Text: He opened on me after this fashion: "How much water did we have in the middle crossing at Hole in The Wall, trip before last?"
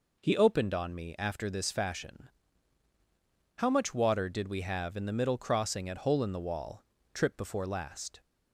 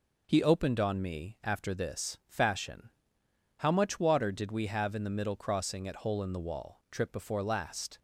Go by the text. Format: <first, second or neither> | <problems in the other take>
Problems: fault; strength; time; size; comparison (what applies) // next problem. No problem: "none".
neither | none